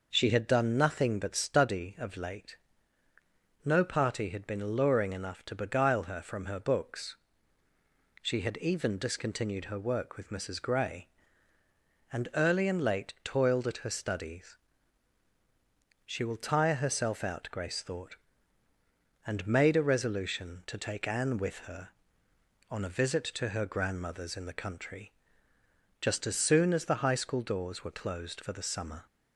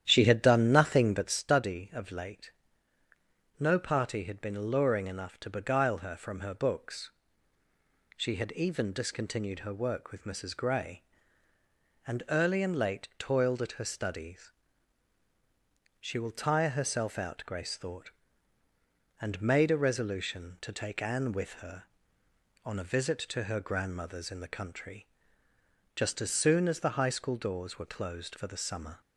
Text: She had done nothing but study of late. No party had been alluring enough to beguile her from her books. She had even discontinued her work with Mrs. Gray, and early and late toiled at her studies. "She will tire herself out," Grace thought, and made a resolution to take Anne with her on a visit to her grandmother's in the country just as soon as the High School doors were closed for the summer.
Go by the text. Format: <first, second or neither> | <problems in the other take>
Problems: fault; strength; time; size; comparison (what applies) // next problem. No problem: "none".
first | starts louder than the rest; strong; until 1.4 s; 10.5 dB // pauses between "country" and "just"; noticeable; at 25.0 s; 0.88 s long; noticeable in the first